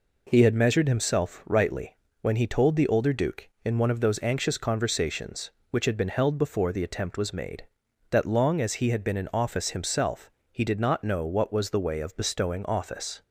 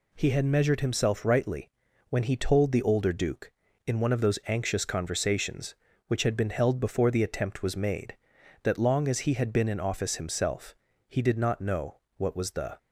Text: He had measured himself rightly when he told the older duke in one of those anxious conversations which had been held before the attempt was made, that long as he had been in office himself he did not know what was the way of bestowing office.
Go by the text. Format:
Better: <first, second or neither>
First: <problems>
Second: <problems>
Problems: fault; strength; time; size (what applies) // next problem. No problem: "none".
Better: first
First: pauses between "rightly" and "when"; slight; at 1.9 s; 0.24 s long // pauses between "himself" and "he"; slight; at 10.2 s; 0.22 s long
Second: pauses between "rightly" and "when"; at 1.6 s; 0.40 s long // pauses between "himself" and "he"; slight; at 10.7 s; 0.32 s long // pauses between "know" and "what"; slight; at 11.9 s; 0.20 s long // stops before "way of bestowing office"; at 12.7 s